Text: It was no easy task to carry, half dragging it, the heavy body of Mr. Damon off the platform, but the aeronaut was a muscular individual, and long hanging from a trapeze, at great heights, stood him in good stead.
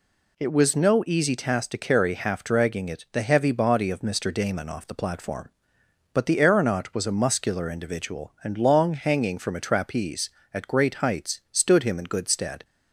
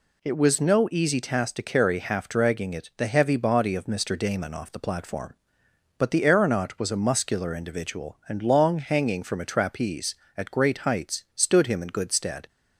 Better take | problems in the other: neither | none

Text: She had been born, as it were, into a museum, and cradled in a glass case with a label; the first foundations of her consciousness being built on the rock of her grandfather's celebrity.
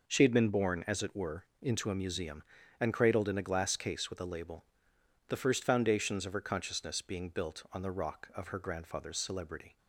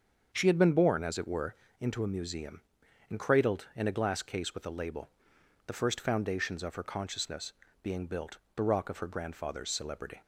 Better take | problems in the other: first | starts louder than the rest; until 1.3 s; 7 dB // pauses between "consciousness" and "being"; slight; at 7.5 s; 0.30 s long // skips "on"; at 8.4 s

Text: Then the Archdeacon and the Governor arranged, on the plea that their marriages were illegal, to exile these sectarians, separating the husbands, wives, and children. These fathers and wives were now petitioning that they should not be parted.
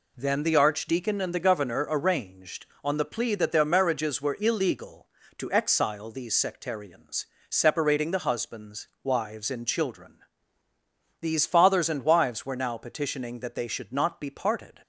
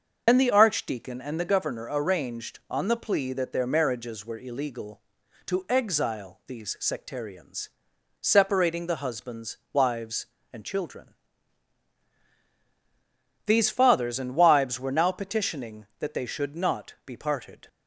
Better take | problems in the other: first | loses the start of "Then"; at 0.2 s; 80 ms // starts louder than the rest; until 1.2 s; 6.5 dB

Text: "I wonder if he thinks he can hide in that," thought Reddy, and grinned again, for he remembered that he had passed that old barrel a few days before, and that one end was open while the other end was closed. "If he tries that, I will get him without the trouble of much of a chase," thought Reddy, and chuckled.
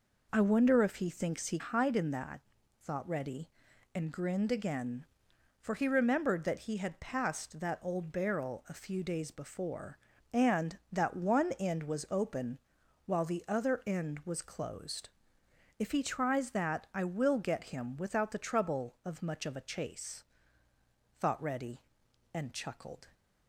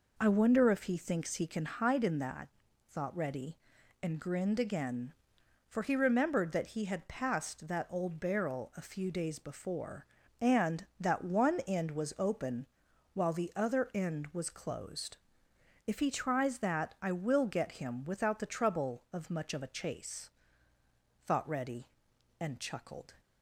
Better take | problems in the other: second | skips "can"; at 1.5 s // pauses between "open" and "while"; noticeable; at 12.5 s; 0.48 s long; noticeable in the second

